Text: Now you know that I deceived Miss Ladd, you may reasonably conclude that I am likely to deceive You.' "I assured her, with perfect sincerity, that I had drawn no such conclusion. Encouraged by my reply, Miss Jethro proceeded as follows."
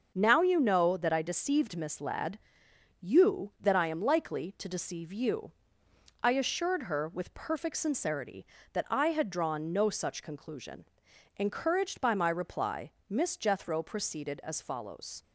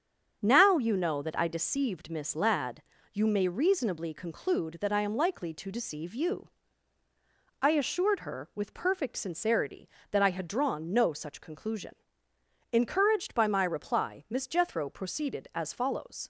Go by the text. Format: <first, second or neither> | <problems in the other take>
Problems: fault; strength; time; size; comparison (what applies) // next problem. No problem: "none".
second | starts louder than the rest; until 1.1 s; 6.5 dB; strong in the second // skips "may reasonably conclude"; at 3.5 s